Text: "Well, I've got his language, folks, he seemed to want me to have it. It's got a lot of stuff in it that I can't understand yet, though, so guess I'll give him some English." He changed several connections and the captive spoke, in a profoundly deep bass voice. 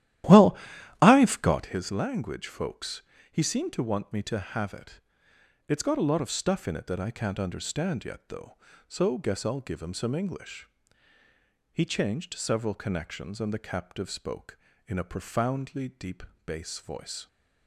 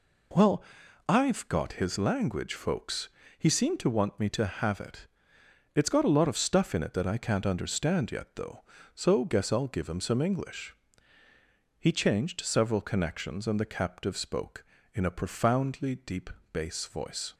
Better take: second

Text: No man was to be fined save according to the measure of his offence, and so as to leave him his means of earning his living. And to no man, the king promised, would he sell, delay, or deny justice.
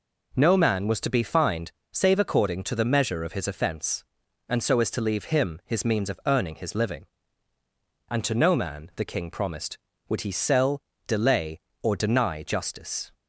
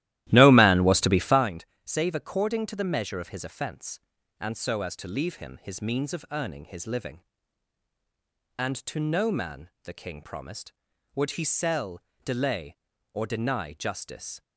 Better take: first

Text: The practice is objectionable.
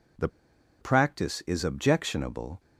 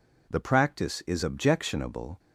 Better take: second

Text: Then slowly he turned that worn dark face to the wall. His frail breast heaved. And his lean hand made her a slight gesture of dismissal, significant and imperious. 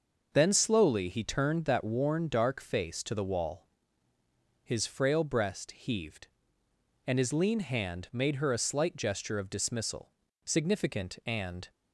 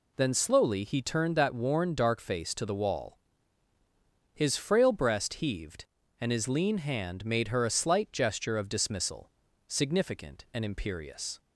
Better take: second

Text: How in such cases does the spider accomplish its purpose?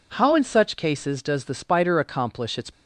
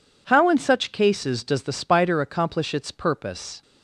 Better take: second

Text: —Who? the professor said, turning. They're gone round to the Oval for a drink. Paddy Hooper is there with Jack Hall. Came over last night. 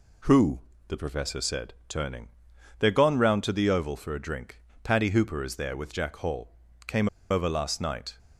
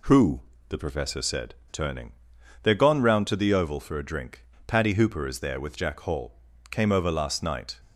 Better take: second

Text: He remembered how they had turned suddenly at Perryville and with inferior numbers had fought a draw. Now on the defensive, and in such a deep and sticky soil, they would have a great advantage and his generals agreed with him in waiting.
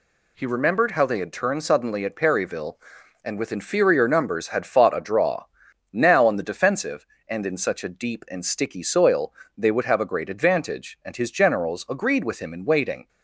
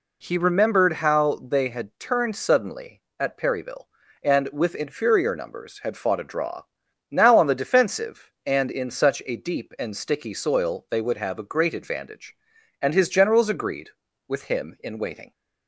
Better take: neither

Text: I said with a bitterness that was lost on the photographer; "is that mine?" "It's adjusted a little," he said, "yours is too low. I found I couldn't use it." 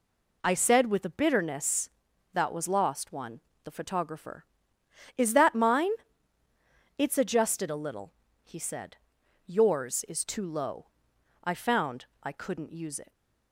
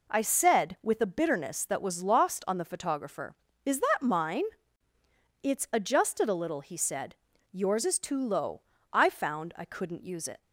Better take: second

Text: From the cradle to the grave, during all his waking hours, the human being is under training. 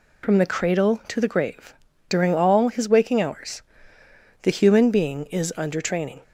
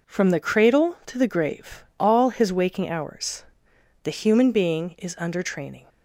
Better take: first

